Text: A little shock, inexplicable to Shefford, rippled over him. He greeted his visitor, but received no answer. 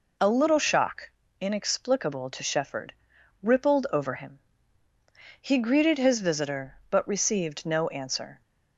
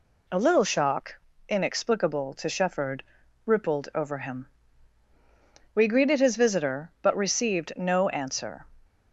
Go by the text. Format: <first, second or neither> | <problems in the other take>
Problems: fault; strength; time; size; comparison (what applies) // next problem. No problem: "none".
first | says "We" for "He"; at 5.7 s